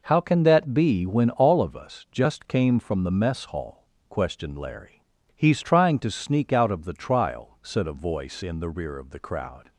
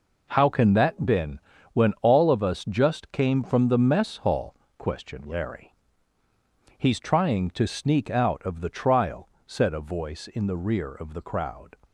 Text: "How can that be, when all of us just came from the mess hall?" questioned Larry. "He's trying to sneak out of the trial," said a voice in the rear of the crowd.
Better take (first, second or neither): first